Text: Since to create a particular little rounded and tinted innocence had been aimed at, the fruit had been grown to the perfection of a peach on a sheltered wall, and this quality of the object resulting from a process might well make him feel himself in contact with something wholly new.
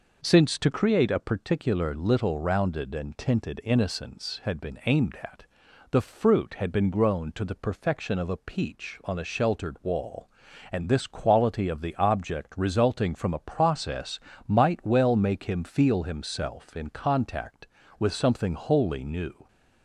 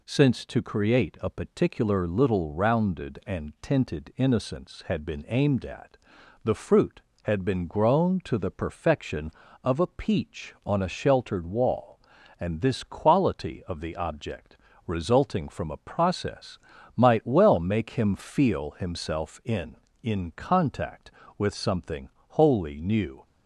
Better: first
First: pauses between "process" and "might"; slight; at 14.1 s; 0.28 s long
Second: pauses between "object" and "resulting"; slight; at 14.5 s; 0.30 s long // pauses between "process" and "might"; at 16.5 s; 0.38 s long // says "in" twice; at 20.0 s // pauses between "something" and "wholly"; slight; at 22.0 s; 0.18 s long

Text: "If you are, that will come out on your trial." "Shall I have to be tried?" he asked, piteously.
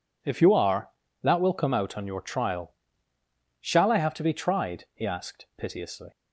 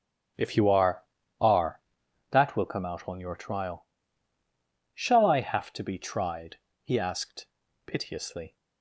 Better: first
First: none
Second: starts louder than the rest; strong; until 1.7 s; 8 dB // says "are" twice; at 1.4 s

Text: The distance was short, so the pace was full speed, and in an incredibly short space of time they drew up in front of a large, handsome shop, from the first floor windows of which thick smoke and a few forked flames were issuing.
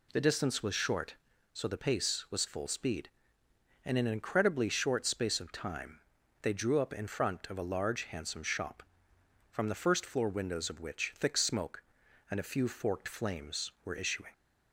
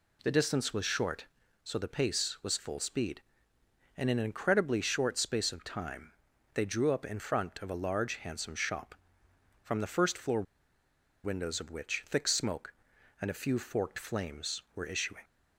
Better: first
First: pauses between "time" and "they"; at 6.0 s; 0.40 s long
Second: pauses between "time" and "they"; at 6.1 s; 0.40 s long // pauses between "floor" and "windows"; noticeable; at 10.4 s; 0.81 s long

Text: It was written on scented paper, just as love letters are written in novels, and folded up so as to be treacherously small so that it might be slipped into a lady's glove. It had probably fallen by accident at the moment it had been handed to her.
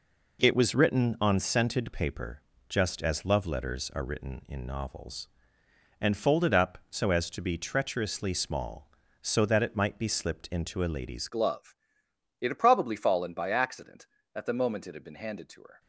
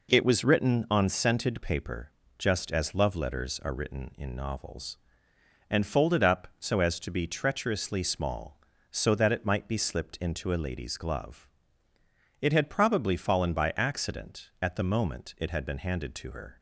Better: second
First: changes voice at "glove"; from 11.2 s on; 4.5 s long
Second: none

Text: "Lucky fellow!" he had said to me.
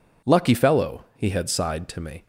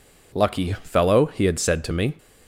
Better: second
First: says "sighed" for "said"; at 1.4 s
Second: none

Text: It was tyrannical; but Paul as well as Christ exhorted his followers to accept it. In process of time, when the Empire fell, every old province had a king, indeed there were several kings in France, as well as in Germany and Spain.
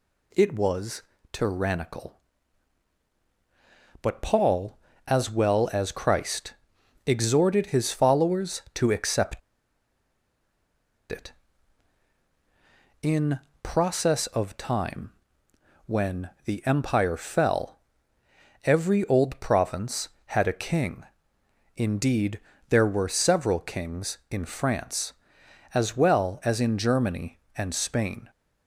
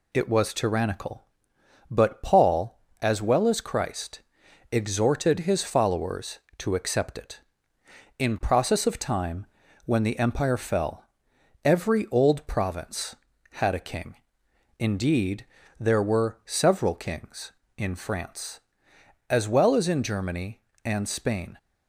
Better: second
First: pauses between "was" and "tyrannical"; slight; at 1.0 s; 0.30 s long // pauses between "Christ" and "exhorted"; noticeable; at 6.5 s; 0.52 s long // pauses between "accept" and "it"; strong; at 9.3 s; 1.7 s long // pauses between "In" and "process"; slight; at 13.3 s; 0.22 s long // pauses between "when" and "the"; slight; at 16.2 s; 0.16 s long // pauses between "indeed" and "there"; slight; at 22.3 s; 0.30 s long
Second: pauses between "Christ" and "exhorted"; noticeable; at 4.1 s; 0.50 s long // pauses between "indeed" and "there"; slight; at 15.4 s; 0.34 s long

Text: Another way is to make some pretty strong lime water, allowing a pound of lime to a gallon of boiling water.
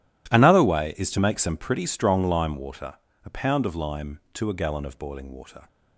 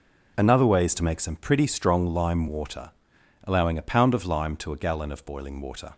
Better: second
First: skips "allowing"; at 3.1 s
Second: none

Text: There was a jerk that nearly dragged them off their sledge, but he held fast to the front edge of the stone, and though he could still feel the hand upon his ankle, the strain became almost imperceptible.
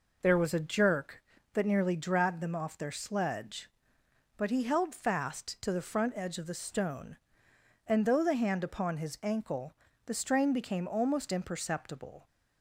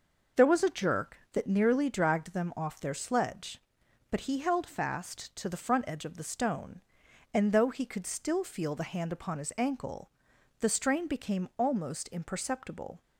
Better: second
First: skips "he could still feel"; at 8.2 s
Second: none

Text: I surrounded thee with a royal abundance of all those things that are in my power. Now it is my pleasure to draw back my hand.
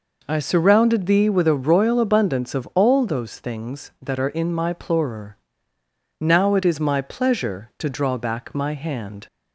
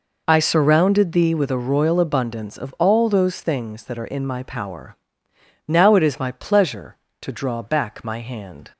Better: second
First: says "plorer" for "power"; at 4.7 s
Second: none

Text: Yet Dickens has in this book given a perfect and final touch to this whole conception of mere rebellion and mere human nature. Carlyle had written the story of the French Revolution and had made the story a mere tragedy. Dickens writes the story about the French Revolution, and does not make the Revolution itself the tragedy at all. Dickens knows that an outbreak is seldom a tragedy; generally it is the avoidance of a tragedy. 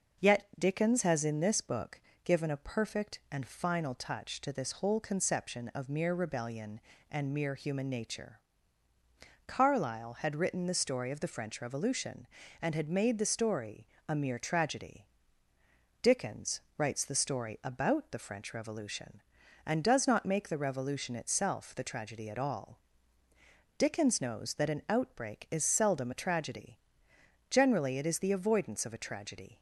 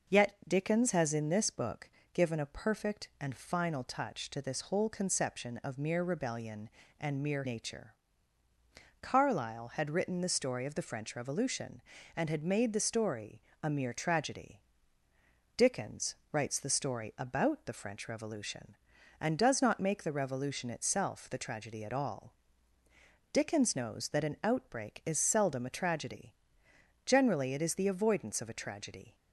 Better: first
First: pauses between "book" and "given"; slight; at 2.0 s; 0.24 s long // pauses between "story" and "a"; slight; at 13.8 s; 0.20 s long // pauses between "Dickens" and "writes"; slight; at 16.6 s; 0.16 s long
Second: pauses between "book" and "given"; slight; at 1.8 s; 0.24 s long // skips "human"; at 7.4 s // pauses between "story" and "a"; slight; at 13.4 s; 0.20 s long // pauses between "Dickens" and "writes"; slight; at 16.1 s; 0.16 s long

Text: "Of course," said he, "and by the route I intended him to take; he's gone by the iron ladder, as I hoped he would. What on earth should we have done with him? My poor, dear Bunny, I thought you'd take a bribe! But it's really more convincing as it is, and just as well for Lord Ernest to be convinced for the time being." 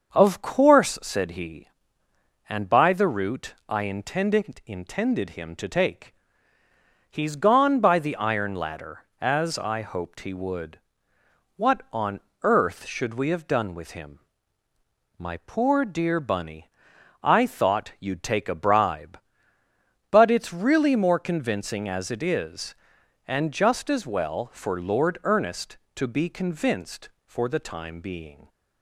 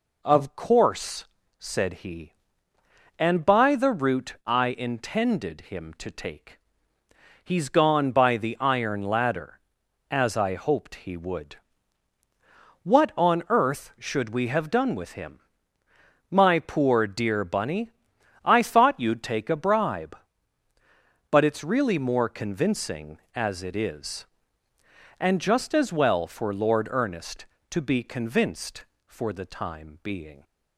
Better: second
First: starts louder than the rest; until 1.1 s; 6.5 dB // says "intended" twice; at 4.6 s // pauses between "on" and "earth"; slight; at 12.2 s; 0.22 s long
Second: none

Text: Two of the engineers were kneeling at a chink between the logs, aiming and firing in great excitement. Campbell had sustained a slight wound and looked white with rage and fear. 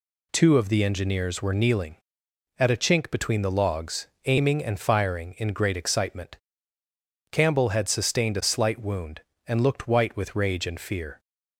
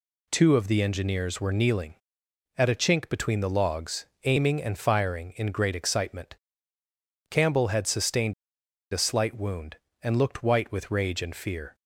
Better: first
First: none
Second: pauses between "sustained" and "a"; noticeable; at 8.3 s; 0.59 s long

